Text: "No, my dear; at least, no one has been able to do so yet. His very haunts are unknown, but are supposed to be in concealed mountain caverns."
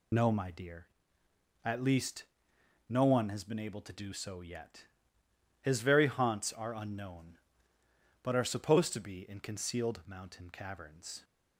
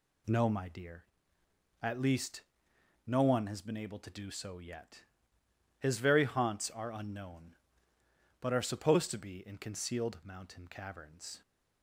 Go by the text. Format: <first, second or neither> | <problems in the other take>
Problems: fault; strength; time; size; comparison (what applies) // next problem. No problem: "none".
second | loses the start of "No"; at 0.1 s; 35 ms